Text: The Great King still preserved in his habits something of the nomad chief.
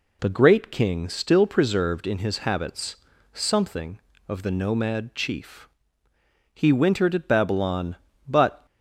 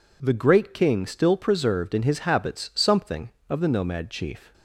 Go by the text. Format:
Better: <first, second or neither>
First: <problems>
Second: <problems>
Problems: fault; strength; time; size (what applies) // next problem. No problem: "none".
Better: second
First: pauses between "habits" and "something"; slight; at 2.9 s; 0.36 s long // goes on to say "He wintered at Babylon but"; strong; from 6.5 s on; 2.1 s long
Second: none